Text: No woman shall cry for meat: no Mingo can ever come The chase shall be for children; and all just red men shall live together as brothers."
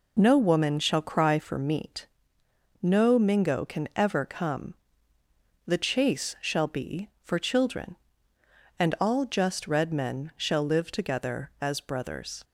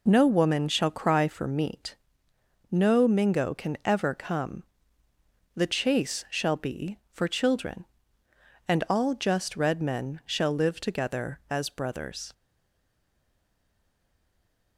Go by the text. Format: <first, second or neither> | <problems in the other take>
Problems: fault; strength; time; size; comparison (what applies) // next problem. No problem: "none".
first | pauses between "come" and "The"; noticeable; at 4.6 s; 0.92 s long; noticeable in the first // stays silent after the last word; from 12.3 s on; 2.4 s long